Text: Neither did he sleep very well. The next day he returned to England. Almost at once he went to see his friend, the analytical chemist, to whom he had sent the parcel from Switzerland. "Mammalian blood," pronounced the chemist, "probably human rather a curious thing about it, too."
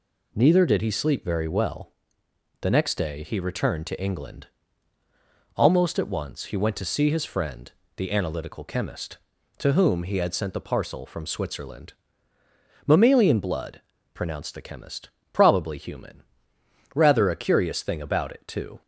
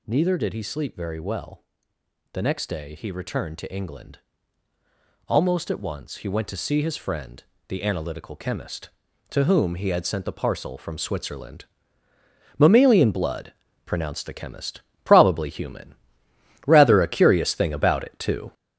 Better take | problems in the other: first | gets louder; noticeable; throughout; 5.5 dB // pauses between "human" and "rather"; noticeable; at 15.9 s; 0.70 s long; noticeable in the first

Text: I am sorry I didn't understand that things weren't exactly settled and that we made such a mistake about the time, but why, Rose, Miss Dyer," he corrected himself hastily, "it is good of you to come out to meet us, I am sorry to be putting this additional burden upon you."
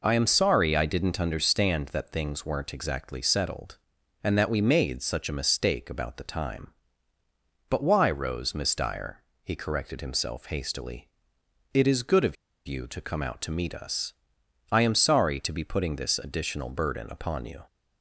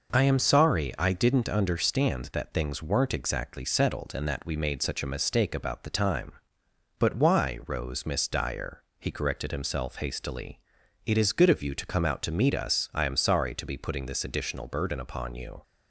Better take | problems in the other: second | pauses between "of" and "you"; slight; at 12.3 s; 0.31 s long

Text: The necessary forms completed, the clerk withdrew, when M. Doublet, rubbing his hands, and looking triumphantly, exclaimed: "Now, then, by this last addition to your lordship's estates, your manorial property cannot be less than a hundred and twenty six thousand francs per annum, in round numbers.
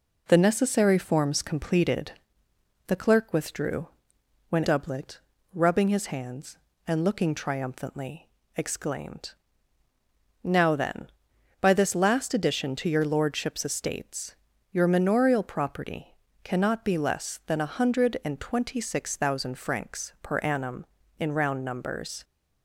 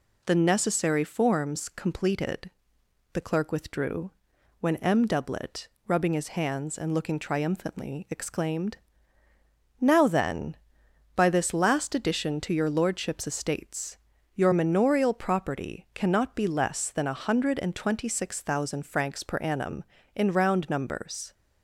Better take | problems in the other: second | skips "M"; at 4.6 s // pauses between "property" and "cannot"; slight; at 16.1 s; 0.26 s long

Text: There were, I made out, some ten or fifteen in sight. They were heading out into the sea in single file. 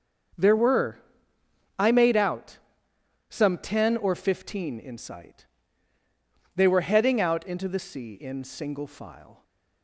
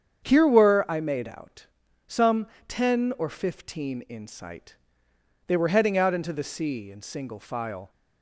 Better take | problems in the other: first | starts louder than the rest; strong; until 1.2 s; 7.5 dB; also in the first // says "Here" for "There"; at 0.2 s // pauses between "some" and "ten"; slight; at 2.4 s; 0.22 s long

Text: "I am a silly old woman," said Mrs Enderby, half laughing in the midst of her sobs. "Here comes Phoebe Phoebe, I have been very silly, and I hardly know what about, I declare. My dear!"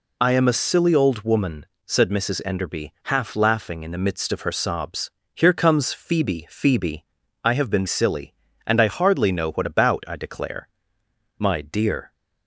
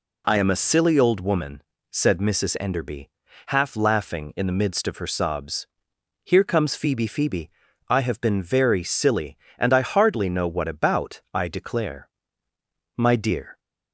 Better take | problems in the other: second | skips "very"; at 7.8 s

